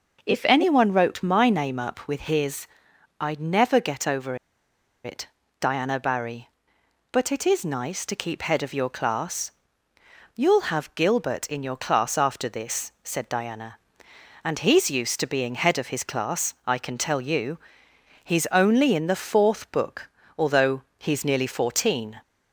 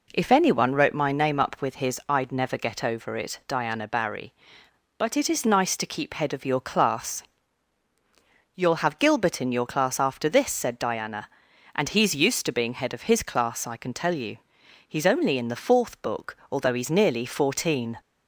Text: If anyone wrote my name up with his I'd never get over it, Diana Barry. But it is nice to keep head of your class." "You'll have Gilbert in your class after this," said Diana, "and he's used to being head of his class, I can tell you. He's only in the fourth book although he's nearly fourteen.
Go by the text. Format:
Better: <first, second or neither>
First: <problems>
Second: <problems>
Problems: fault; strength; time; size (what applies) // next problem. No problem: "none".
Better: second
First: pauses between "his" and "I'd"; noticeable; at 2.6 s; 0.52 s long // pauses between "over" and "it"; noticeable; at 4.3 s; 0.68 s long // pauses between "book" and "although"; slight; at 20.0 s; 0.30 s long // pauses between "although" and "he's"; slight; at 20.8 s; 0.16 s long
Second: pauses between "book" and "although"; slight; at 16.3 s; 0.16 s long